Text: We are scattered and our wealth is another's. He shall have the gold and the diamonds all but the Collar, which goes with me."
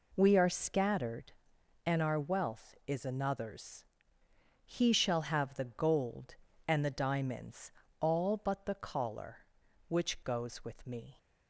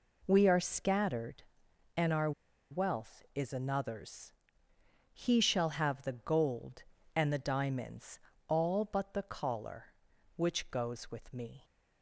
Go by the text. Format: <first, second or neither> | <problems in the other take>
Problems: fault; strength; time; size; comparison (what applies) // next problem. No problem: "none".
first | pauses between "our" and "wealth"; at 2.3 s; 0.39 s long // pauses between "diamonds" and "all"; slight; at 8.1 s; 0.28 s long; slight in the first